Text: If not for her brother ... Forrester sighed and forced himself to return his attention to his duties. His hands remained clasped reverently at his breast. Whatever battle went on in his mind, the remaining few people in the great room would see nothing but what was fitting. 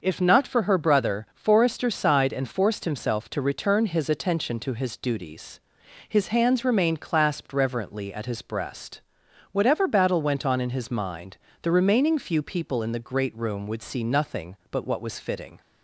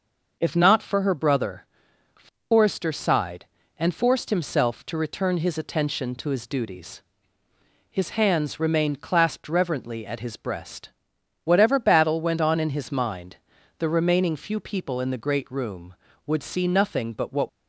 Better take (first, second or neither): first